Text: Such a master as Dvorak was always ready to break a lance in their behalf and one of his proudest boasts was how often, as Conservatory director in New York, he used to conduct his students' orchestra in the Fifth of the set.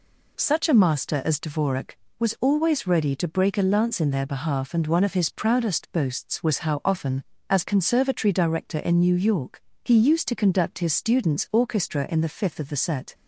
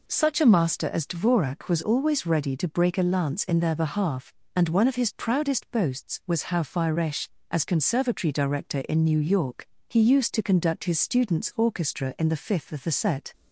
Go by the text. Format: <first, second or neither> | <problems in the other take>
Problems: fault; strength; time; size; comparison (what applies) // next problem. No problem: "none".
first | says "firesh" for "often"; at 6.6 s